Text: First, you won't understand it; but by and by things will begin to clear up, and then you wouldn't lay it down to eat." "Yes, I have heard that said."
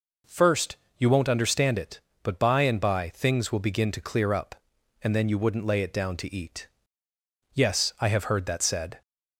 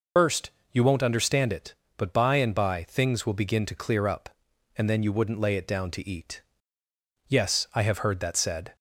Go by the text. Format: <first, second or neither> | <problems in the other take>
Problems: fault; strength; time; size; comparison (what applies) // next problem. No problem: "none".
first | loses the start of "First"; at 0.1 s; 165 ms